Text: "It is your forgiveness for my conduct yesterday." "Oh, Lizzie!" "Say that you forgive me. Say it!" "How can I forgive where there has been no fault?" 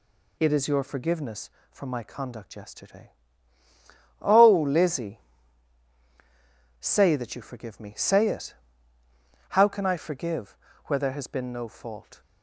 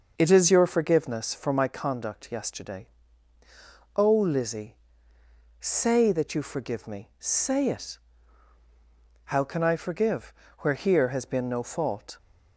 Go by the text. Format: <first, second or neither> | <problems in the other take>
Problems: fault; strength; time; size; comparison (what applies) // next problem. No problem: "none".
first | pauses between "forgive" and "where"; slight; at 10.3 s; 0.26 s long; slight in the first // says "here" for "there"; at 10.7 s